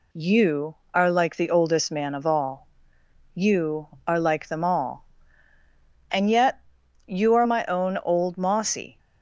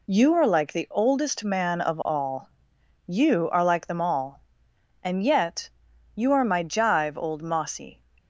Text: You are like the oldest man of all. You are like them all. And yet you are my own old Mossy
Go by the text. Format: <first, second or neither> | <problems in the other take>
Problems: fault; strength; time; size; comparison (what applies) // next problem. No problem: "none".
first | pauses between "yet" and "you"; at 5.7 s; 0.44 s long; noticeable in the first // says "jive" for "own"; at 6.6 s